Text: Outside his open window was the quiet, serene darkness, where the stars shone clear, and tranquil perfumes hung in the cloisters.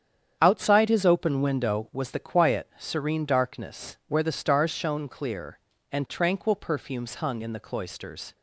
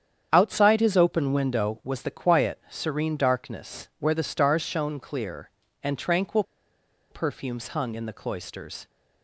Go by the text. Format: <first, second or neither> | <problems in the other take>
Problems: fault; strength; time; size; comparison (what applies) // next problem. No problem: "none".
first | starts louder than the rest; strong; until 1.3 s; 8.5 dB; strong in the first // pauses between "tranquil" and "perfumes"; noticeable; at 6.4 s; 0.67 s long